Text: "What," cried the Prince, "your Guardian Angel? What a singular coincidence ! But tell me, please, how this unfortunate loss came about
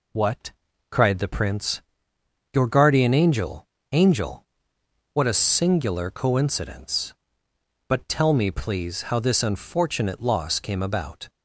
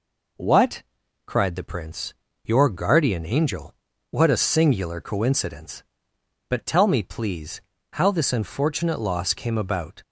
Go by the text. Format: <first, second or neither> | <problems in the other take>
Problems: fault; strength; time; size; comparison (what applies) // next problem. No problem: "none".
second | says "Angel" twice; at 3.9 s